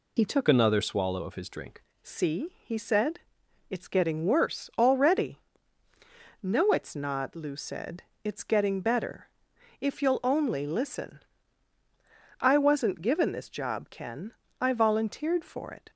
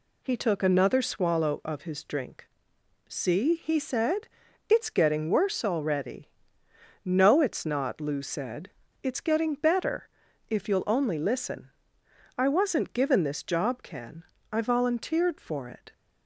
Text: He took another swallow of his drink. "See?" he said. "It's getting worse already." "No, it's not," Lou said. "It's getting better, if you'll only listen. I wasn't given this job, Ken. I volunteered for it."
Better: second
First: changes voice from "another" to "drink"; from 0.4 to 1.8 s; 1.4 s long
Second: none

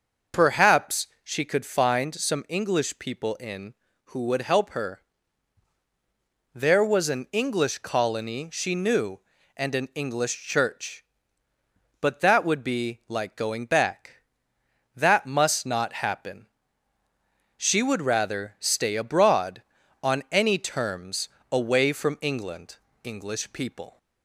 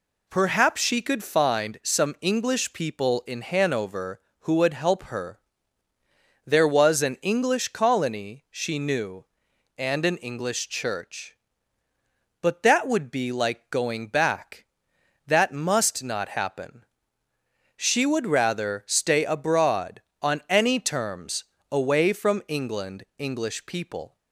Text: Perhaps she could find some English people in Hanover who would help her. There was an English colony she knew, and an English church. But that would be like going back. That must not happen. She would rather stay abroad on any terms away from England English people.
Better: second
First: starts louder than the rest; noticeable; until 1.5 s; 6 dB // pauses between "Perhaps" and "she"; slight; at 1.0 s; 0.16 s long // skips "Hanover"; at 3.8 s // pauses between "terms" and "away"; slight; at 21.2 s; 0.24 s long // pauses between "England" and "English"; slight; at 22.7 s; 0.26 s long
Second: pauses between "terms" and "away"; slight; at 21.4 s; 0.28 s long

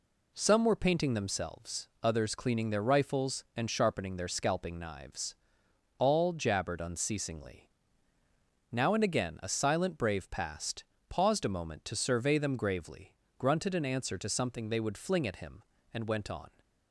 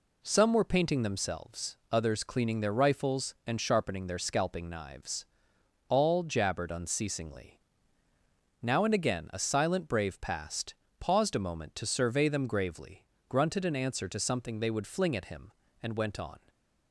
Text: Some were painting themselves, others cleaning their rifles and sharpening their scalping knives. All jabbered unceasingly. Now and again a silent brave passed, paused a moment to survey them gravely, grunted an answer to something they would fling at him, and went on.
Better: neither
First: none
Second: none

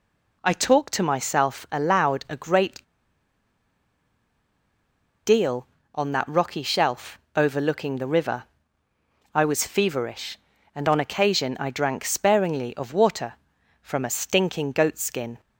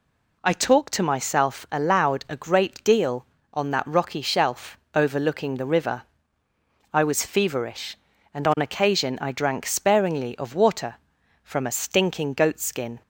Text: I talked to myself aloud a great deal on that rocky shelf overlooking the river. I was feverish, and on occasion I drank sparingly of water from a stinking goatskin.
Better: second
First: pauses between "great" and "deal"; strong; at 2.8 s; 2.4 s long // pauses between "shelf" and "overlooking"; slight; at 7.1 s; 0.18 s long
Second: pauses between "shelf" and "overlooking"; slight; at 4.7 s; 0.18 s long

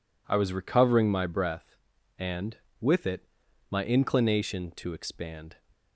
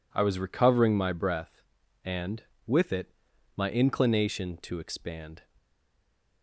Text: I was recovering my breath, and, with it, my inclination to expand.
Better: first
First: none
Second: stays silent after the last word; slight; from 5.5 s on; 0.9 s long

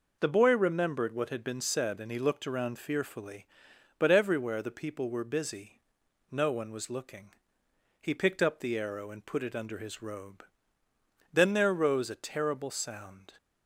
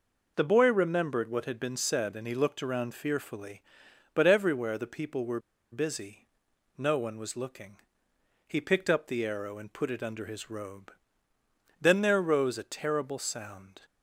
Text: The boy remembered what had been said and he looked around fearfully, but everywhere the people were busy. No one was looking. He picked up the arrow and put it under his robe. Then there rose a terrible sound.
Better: first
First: none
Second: pauses between "were" and "busy"; slight; at 5.4 s; 0.31 s long

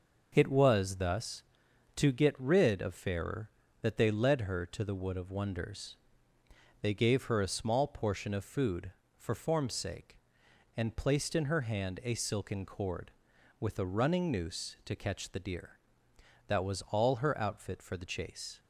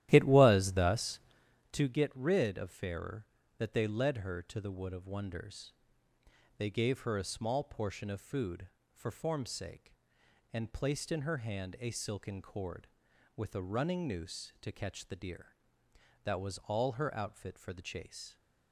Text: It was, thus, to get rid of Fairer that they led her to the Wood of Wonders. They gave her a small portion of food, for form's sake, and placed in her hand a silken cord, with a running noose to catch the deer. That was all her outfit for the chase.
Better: first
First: none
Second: starts louder than the rest; strong; until 1.6 s; 13.5 dB

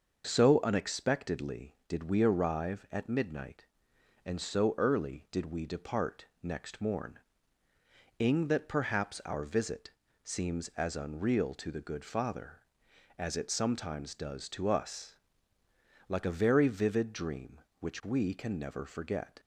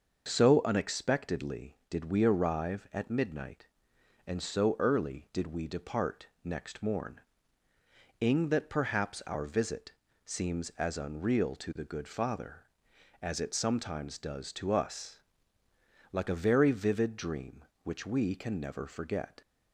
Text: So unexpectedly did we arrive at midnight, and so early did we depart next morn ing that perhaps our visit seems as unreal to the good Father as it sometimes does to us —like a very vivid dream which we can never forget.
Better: neither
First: starts louder than the rest; until 1.3 s; 6 dB // pauses between "depart" and "next"; slight; at 6.2 s; 0.16 s long // pauses between "morn" and "ing"; noticeable; at 7.1 s; 0.98 s long // pauses between "visit" and "seems"; slight; at 9.9 s; 0.32 s long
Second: starts louder than the rest; until 1.3 s; 6 dB // pauses between "depart" and "next"; slight; at 6.2 s; 0.16 s long // pauses between "morn" and "ing"; noticeable; at 7.2 s; 0.98 s long // pauses between "visit" and "seems"; slight; at 9.9 s; 0.32 s long

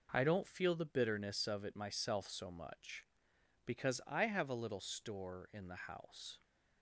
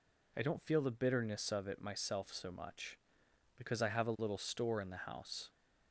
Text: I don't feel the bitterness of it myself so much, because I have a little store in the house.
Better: neither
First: none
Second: none

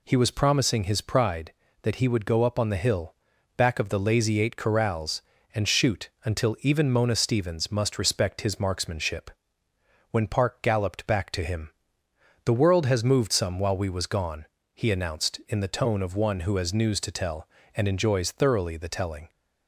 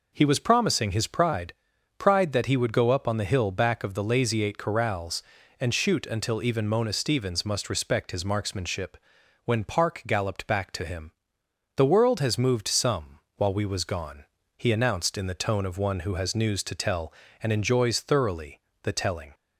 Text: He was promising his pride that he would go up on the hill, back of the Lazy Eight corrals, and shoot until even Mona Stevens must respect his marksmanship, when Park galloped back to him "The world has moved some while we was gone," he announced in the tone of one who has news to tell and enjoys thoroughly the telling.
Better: first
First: pauses between "him" and "The"; noticeable; at 11.6 s; 0.74 s long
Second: says "pride" twice; at 1.9 s // pauses between "him" and "The"; noticeable; at 11.0 s; 0.64 s long // pauses between "some" and "while"; slight; at 13.1 s; 0.20 s long // pauses between "thoroughly" and "the"; slight; at 18.5 s; 0.24 s long

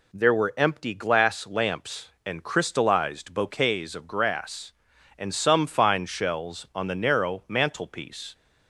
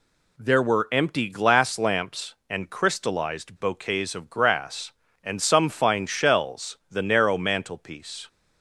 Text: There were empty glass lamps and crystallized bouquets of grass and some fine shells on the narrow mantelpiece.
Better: first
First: none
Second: skips "on"; at 6.8 s

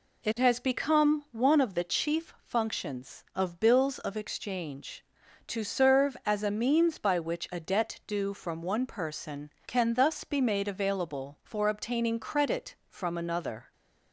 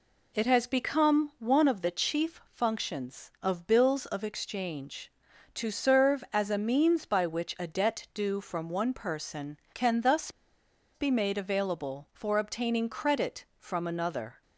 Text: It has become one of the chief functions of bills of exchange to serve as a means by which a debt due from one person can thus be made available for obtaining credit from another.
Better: first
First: none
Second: pauses between "thus" and "be"; noticeable; at 10.2 s; 0.65 s long

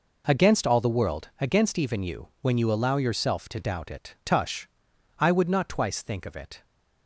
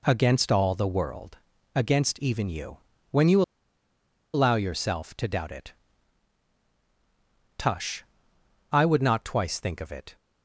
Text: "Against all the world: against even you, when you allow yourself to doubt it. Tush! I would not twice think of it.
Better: first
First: none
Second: pauses between "you" and "allow"; noticeable; at 3.4 s; 0.92 s long

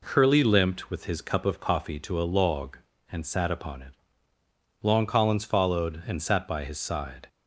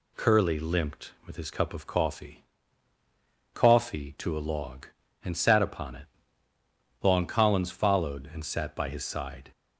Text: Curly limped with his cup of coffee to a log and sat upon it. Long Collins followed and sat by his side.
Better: first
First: none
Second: says "coffee" twice; at 3.5 s

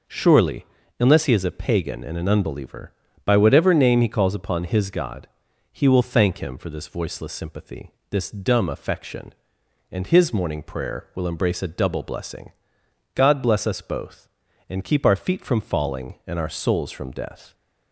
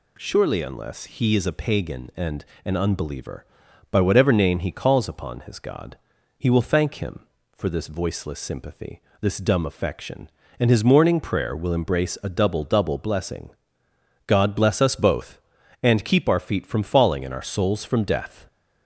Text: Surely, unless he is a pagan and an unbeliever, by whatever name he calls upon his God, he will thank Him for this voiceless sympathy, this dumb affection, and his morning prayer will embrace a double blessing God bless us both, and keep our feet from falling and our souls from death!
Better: first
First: pauses between "blessing" and "God"; noticeable; at 12.5 s; 0.62 s long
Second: pauses between "and" and "an"; slight; at 2.4 s; 0.22 s long // says "double" twice; at 12.6 s // pauses between "blessing" and "God"; noticeable; at 13.4 s; 0.76 s long

